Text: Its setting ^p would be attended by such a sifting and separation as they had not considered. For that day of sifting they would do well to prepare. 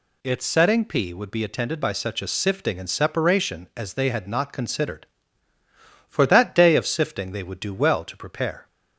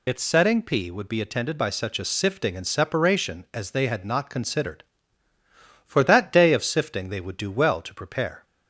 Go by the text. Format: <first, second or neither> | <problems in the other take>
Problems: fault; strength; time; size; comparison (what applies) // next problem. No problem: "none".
first | loses the start of "Its"; at 0.0 s; 75 ms